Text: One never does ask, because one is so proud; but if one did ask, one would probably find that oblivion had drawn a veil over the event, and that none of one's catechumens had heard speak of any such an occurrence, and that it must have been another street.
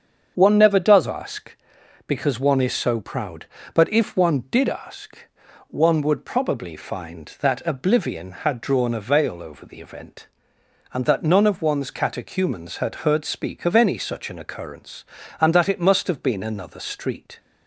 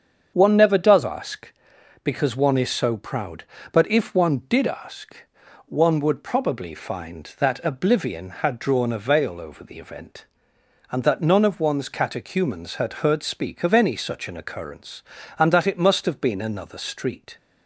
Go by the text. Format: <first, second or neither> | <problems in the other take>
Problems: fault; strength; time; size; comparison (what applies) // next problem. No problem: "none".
neither | starts louder than the rest; strong; the same in both